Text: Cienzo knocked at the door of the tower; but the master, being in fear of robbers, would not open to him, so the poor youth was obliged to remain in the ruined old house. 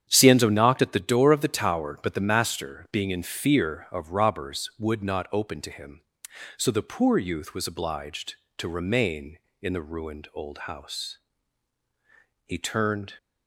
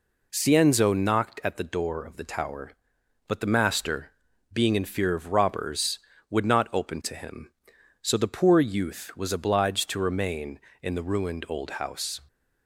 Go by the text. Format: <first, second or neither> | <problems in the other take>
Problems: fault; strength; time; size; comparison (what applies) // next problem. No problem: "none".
second | starts louder than the rest; strong; until 1.1 s; 9 dB // goes on to say "He turned"; noticeable; from 12.4 s on; 0.70 s long